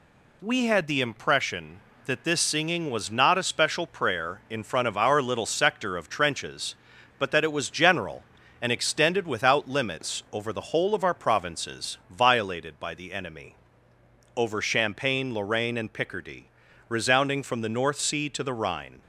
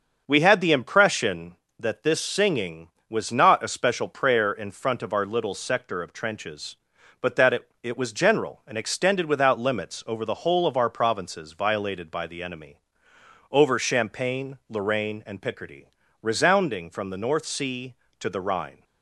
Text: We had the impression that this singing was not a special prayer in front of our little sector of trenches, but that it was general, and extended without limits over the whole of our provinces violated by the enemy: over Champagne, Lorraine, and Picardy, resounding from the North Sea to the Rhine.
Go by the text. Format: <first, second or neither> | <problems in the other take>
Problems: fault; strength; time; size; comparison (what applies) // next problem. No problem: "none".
first | starts louder than the rest; until 1.2 s; 6.5 dB // says "it" twice; at 7.8 s